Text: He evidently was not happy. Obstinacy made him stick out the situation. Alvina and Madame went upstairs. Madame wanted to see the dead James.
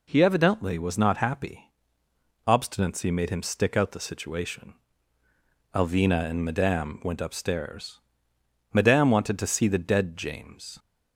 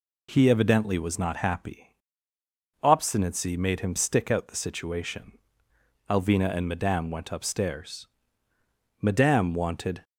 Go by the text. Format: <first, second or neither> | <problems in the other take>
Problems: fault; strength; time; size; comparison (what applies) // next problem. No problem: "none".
first | stops before "to see the dead James"; at 10.0 s